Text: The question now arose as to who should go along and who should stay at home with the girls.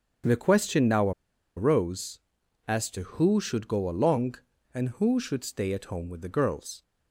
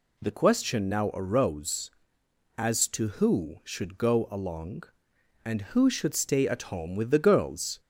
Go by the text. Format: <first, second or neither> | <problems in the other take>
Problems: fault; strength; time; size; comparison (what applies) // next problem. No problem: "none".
second | starts louder than the rest; strong; until 1.7 s; 7.5 dB // pauses between "now" and "arose"; at 1.1 s; 0.45 s long